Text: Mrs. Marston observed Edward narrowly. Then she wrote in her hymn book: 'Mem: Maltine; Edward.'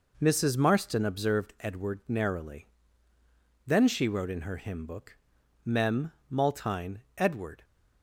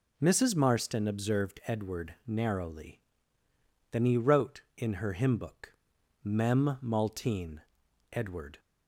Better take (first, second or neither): first